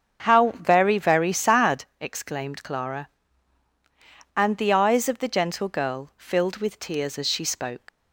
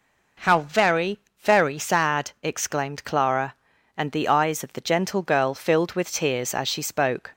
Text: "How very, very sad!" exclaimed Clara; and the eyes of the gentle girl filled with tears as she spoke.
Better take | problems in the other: second | starts louder than the rest; until 1.2 s; 7 dB // leaves "spoke" unfinished; at 7.8 s; 80 ms

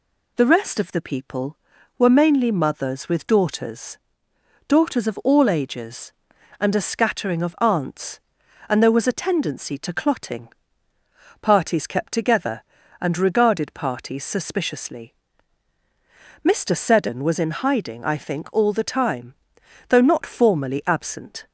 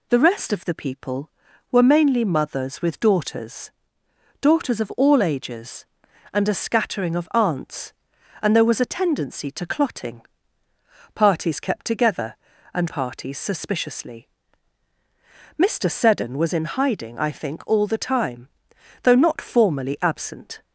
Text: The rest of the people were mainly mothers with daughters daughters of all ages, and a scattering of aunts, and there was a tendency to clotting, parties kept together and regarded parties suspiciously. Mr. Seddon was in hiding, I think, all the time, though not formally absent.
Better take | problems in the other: first | pauses between "daughters" and "daughters"; noticeable; at 3.7 s; 0.68 s long; noticeable in the first // skips "regarded"; at 12.8 s

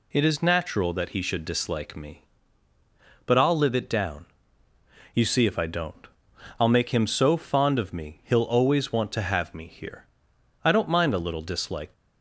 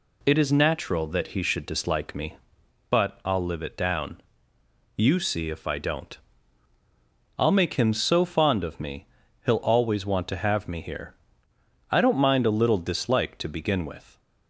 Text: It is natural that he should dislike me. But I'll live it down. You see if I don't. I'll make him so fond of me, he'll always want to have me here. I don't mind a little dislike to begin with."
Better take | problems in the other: second | stops before "to begin with"; at 11.9 s

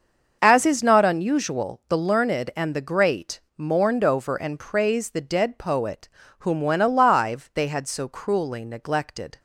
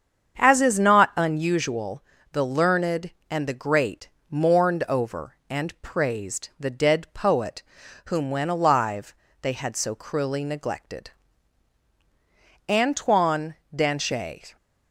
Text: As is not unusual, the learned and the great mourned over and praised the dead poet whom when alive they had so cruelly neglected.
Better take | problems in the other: first | starts louder than the rest; strong; until 1.4 s; 7.5 dB; also in the first // pauses between "great" and "mourned"; slight; at 4.0 s; 0.22 s long; slight in the first // pauses between "poet" and "whom"; at 7.6 s; 0.44 s long; slight in the first // pauses between "alive" and "they"; slight; at 9.1 s; 0.28 s long // goes on to say "Antoine Danchet"; strong; from 12.6 s on; 1.8 s long

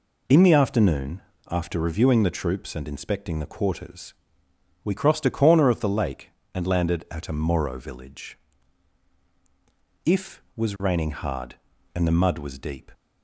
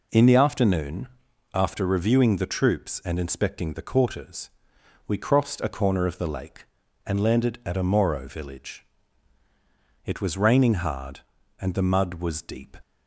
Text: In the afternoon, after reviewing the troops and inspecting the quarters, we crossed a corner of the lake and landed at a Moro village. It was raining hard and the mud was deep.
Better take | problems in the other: second | says "If" for "It"; at 10.0 s

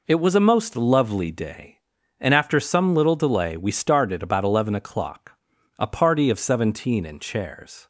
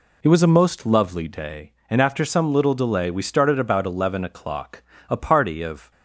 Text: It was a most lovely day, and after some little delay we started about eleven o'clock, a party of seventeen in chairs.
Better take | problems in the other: first | stops before "seventeen in chairs"; at 5.9 s

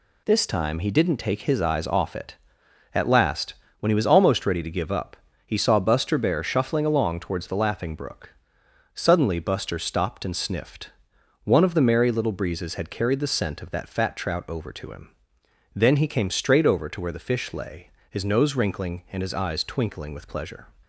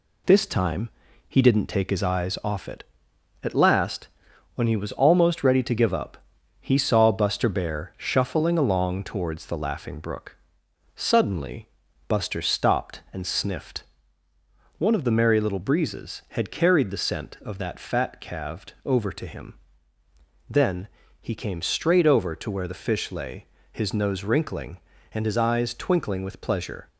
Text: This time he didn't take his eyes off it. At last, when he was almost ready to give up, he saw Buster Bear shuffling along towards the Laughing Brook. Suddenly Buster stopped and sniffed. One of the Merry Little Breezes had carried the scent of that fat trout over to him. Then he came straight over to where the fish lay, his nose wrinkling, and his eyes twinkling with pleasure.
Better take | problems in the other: first | pauses between "time" and "he"; at 0.8 s; 0.38 s long // pauses between "Suddenly" and "Buster"; at 11.6 s; 0.38 s long // says "calved" for "trout"; at 18.1 s // pauses between "Then" and "he"; slight; at 20.8 s; 0.34 s long

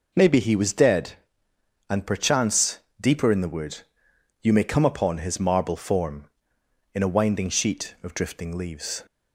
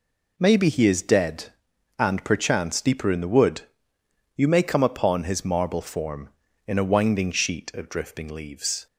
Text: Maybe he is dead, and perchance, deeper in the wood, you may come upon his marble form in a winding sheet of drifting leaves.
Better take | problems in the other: second | says "was" for "is"; at 0.5 s

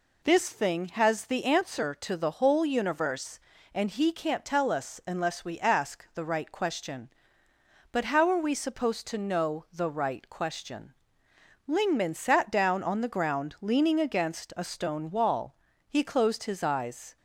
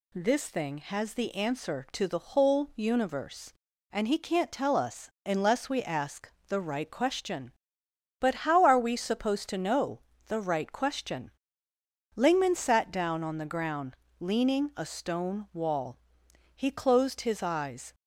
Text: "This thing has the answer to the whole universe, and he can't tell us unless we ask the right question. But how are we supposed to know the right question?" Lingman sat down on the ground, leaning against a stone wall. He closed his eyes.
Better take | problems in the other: first | pauses between "us" and "unless"; slight; at 5.0 s; 0.16 s long // pauses between "ask" and "the"; slight; at 6.3 s; 0.18 s long // pauses between "know" and "the"; slight; at 10.0 s; 0.26 s long // skips "against"; at 14.7 s

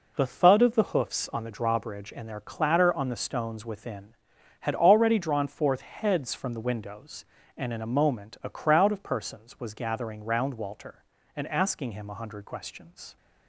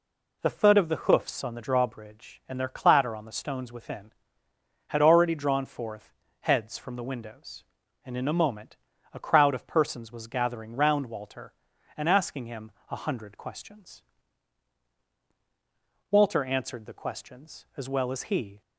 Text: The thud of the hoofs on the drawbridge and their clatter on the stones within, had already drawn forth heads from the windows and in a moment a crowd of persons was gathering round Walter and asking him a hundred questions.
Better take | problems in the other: first | pauses between "forth" and "heads"; slight; at 6.1 s; 0.28 s long // pauses between "moment" and "a"; slight; at 8.7 s; 0.36 s long // pauses between "him" and "a"; slight; at 12.7 s; 0.18 s long // goes on to say "Walter answered the questions as well as he"; strong; from 16.0 s on; 2.5 s long

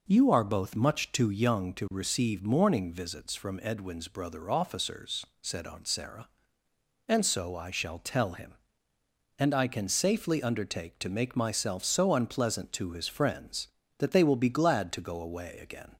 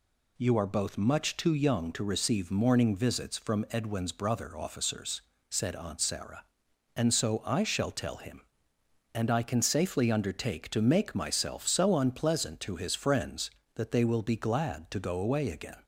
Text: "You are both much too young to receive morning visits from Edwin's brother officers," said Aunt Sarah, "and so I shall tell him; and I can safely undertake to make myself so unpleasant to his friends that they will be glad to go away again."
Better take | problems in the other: neither | none

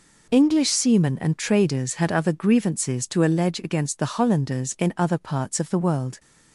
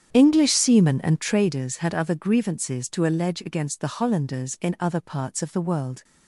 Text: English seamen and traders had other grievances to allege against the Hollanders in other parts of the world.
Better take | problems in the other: first | starts louder than the rest; strong; until 1.5 s; 9 dB

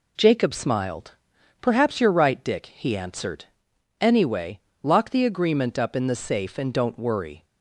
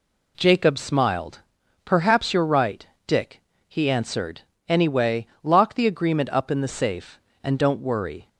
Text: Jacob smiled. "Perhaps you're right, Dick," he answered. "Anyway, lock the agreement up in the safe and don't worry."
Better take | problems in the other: neither | none

